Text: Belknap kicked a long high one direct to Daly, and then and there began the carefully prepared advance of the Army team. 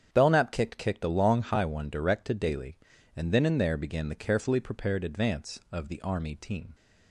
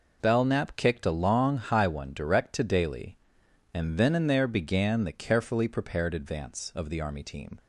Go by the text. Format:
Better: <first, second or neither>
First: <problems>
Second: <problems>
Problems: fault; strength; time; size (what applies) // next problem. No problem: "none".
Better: second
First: starts louder than the rest; strong; until 1.1 s; 8.5 dB // says "kicked" twice; at 0.7 s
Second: none